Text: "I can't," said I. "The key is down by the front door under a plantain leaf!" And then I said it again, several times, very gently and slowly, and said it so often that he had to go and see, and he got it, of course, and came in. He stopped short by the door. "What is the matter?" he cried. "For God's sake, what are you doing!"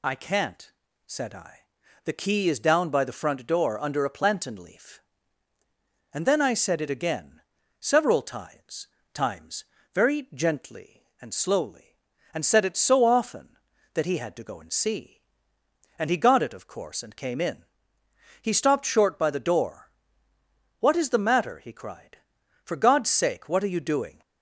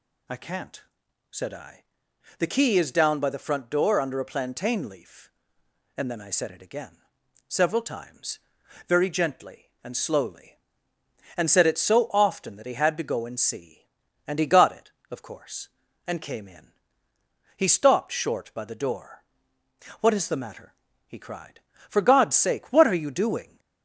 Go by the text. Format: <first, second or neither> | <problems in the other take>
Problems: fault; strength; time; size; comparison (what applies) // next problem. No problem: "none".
second | says "times" twice; at 9.1 s